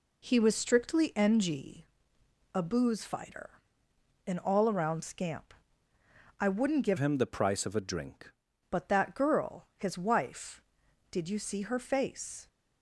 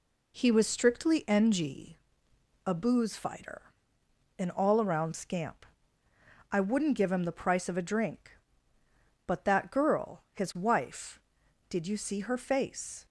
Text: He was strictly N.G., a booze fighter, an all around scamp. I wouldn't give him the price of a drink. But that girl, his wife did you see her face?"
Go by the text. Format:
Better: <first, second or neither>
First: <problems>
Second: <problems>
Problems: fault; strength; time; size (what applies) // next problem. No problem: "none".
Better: second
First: changes voice from "him" to "drink"; from 6.9 to 8.3 s; 1.4 s long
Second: none